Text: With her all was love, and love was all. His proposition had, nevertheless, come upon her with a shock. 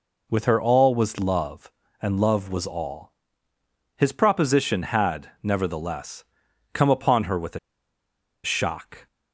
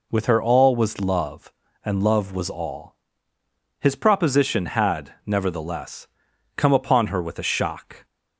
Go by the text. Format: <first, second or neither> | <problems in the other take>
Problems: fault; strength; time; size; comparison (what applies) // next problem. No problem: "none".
second | pauses between "a" and "shock"; noticeable; at 7.5 s; 0.85 s long